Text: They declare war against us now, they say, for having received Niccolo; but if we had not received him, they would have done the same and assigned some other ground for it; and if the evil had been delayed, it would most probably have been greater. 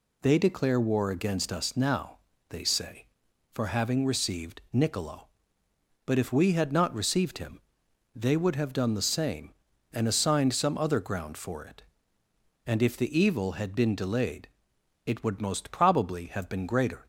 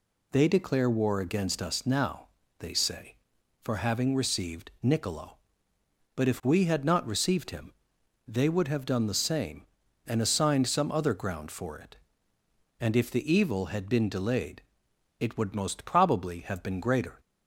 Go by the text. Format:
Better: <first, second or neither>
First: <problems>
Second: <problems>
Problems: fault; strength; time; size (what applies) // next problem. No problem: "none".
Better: neither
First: none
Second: none